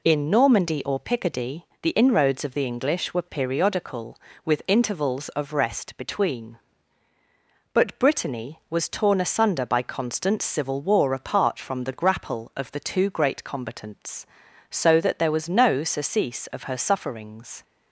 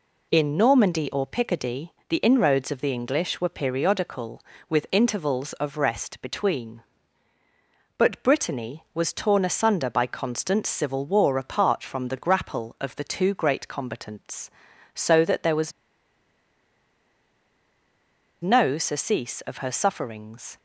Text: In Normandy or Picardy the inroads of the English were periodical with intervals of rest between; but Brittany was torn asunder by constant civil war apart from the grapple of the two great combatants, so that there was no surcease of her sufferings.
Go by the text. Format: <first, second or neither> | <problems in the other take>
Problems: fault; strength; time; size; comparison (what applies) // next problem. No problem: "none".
first | pauses between "Picardy" and "the"; slight; at 1.9 s; 0.18 s long; slight in the first // pauses between "was" and "no"; strong; at 15.7 s; 2.7 s long